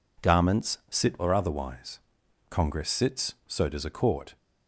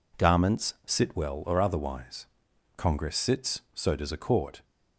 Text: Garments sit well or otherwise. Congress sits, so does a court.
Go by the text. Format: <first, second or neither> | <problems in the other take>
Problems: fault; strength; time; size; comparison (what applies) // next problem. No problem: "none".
second | skips "well"; at 1.1 s